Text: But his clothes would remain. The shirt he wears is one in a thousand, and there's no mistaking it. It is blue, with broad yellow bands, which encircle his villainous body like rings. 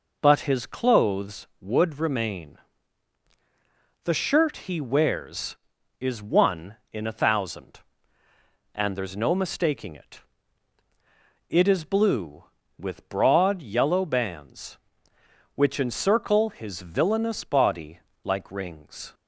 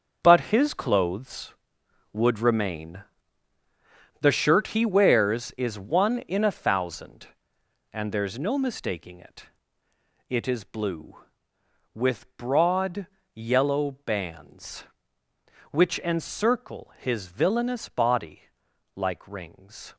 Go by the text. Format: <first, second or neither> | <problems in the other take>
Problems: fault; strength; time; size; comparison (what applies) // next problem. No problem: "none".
first | gets quieter; strong; throughout; 10.5 dB // pauses between "broad" and "yellow"; slight; at 13.0 s; 0.26 s long // pauses between "body" and "like"; noticeable; at 18.4 s; 0.54 s long; slight in the first